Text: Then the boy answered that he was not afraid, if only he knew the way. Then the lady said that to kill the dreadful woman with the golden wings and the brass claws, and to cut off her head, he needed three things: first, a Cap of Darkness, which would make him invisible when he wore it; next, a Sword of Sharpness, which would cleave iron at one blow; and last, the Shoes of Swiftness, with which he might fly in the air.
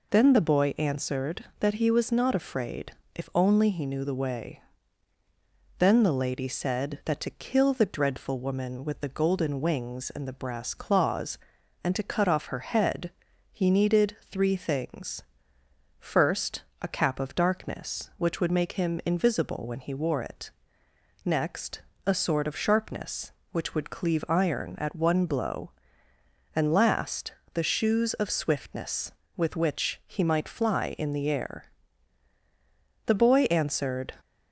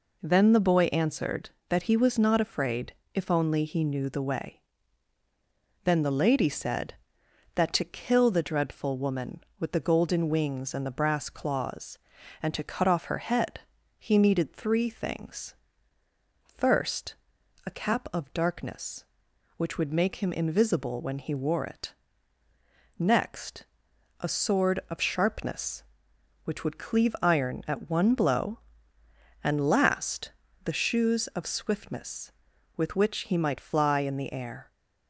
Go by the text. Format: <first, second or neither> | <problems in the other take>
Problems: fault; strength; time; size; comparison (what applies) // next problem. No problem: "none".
second | pauses between "needed" and "three"; slight; at 14.1 s; 0.16 s long // goes on to say "The boy answered"; noticeable; from 33.0 s on; 1.1 s long